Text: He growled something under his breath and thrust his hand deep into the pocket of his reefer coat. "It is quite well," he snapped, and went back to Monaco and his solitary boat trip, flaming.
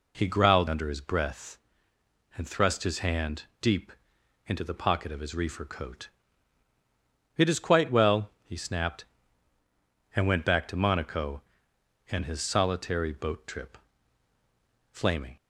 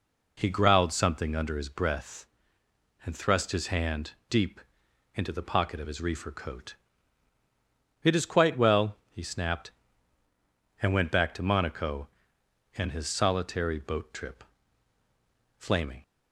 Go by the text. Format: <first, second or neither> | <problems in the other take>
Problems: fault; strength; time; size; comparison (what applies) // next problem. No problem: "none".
second | skips "something"; at 0.6 s // pauses between "hand" and "deep"; slight; at 3.4 s; 0.18 s long; slight in the second // pauses between "deep" and "into"; noticeable; at 3.9 s; 0.56 s long; noticeable in the second